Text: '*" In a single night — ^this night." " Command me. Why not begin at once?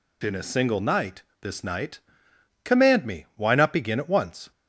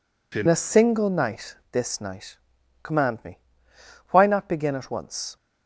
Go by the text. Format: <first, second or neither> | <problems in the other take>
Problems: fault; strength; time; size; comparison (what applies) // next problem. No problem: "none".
first | changes voice at "a"; from 0.4 s on; 4.9 s long